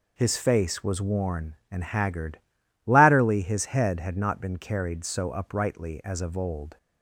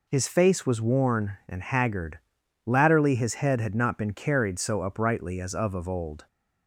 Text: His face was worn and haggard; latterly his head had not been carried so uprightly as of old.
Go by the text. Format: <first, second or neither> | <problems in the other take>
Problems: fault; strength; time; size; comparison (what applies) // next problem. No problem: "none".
first | says "of" twice; at 5.7 s